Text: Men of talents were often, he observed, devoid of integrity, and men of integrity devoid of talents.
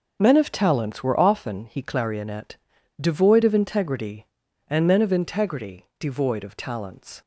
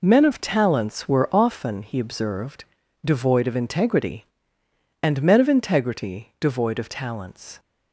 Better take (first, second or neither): second